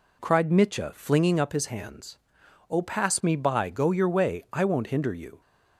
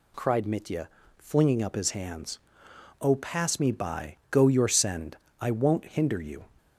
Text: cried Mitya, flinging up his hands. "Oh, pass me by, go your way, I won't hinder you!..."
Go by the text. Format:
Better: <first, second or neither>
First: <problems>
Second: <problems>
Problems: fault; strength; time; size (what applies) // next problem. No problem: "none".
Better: first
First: none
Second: says "send" for "way"; at 4.6 s